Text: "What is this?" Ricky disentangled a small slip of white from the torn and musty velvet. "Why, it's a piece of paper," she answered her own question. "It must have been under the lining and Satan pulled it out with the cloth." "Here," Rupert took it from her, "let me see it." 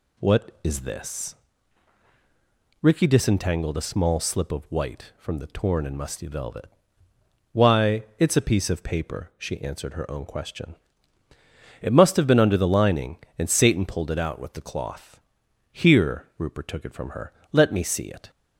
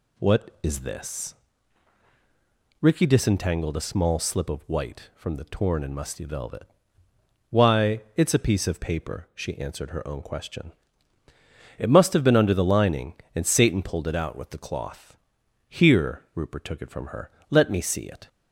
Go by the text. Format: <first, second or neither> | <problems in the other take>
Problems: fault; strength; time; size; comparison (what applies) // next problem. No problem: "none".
neither | none